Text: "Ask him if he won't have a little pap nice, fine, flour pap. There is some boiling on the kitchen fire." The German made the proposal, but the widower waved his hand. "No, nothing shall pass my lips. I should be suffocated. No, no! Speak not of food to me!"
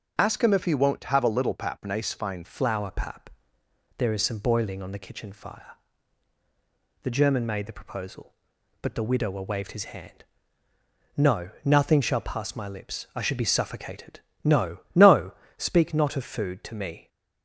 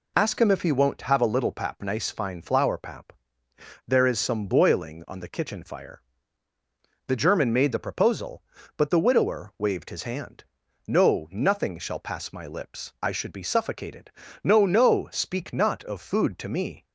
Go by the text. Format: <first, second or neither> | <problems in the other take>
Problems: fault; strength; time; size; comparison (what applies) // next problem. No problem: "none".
second | starts louder than the rest; until 1.1 s; 6.5 dB // changes voice at "flour"; from 2.4 s on; 14.6 s long